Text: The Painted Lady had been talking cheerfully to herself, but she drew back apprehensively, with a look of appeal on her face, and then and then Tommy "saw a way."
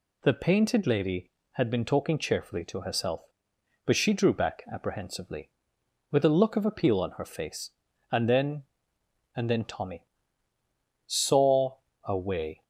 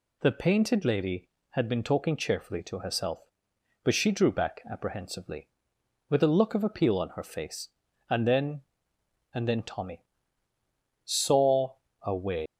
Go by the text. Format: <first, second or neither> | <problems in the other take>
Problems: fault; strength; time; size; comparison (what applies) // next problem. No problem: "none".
first | pauses between "Tommy" and "saw"; at 10.0 s; 1.0 s long; also in the first // pauses between "saw" and "a"; slight; at 11.7 s; 0.26 s long; slight in the first // leaves "way" unfinished; at 12.4 s; 150 ms